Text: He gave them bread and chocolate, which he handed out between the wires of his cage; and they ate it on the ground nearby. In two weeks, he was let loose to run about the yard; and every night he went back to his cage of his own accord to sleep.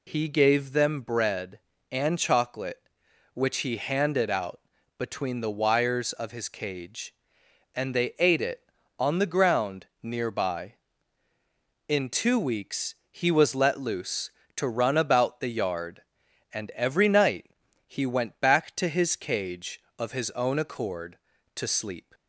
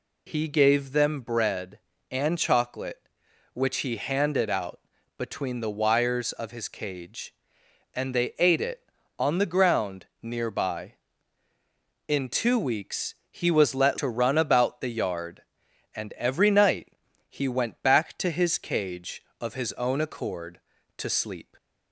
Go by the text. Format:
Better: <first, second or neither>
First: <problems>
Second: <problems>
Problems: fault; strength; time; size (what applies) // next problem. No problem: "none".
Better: first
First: pauses between "out" and "between"; at 4.5 s; 0.38 s long // pauses between "ground" and "nearby"; slight; at 9.8 s; 0.16 s long // pauses between "night" and "he"; at 17.5 s; 0.38 s long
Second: pauses between "out" and "between"; at 4.7 s; 0.38 s long // pauses between "ground" and "nearby"; slight; at 10.0 s; 0.16 s long // skips "loose"; at 13.9 s // pauses between "night" and "he"; at 16.9 s; 0.38 s long